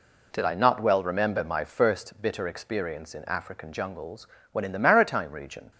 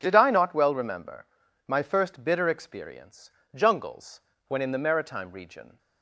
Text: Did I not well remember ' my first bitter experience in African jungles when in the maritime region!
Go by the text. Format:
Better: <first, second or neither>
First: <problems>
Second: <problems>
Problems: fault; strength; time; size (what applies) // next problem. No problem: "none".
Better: first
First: pauses between "jungles" and "when"; slight; at 4.2 s; 0.24 s long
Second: starts louder than the rest; until 1.0 s; 7 dB // skips "in African"; at 3.4 s // pauses between "jungles" and "when"; slight; at 4.1 s; 0.28 s long